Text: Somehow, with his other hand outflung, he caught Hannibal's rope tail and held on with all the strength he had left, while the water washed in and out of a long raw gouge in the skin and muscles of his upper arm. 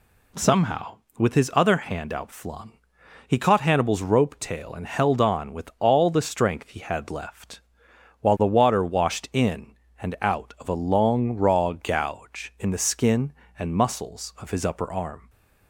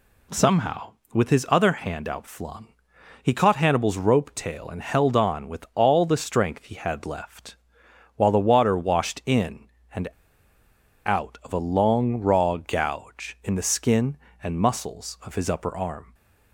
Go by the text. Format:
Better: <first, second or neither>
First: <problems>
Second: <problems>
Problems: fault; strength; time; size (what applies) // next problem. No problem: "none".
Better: first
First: none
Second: pauses between "and" and "out"; at 10.0 s; 0.98 s long